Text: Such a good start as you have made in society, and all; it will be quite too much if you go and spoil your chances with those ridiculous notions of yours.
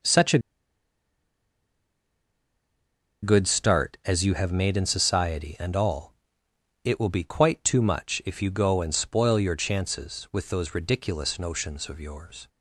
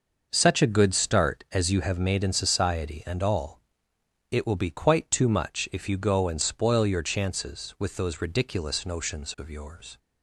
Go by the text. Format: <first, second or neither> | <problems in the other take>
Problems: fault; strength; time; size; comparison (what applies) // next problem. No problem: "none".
second | pauses between "a" and "good"; strong; at 0.3 s; 2.8 s long